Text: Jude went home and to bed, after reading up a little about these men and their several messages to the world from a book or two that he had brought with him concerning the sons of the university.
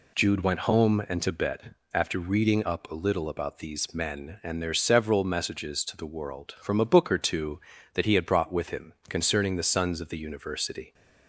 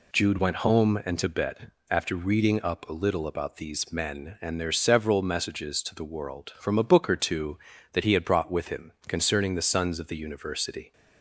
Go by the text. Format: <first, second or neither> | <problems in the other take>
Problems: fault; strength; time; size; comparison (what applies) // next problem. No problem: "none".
neither | pauses between "him" and "concerning"; slight; the same in both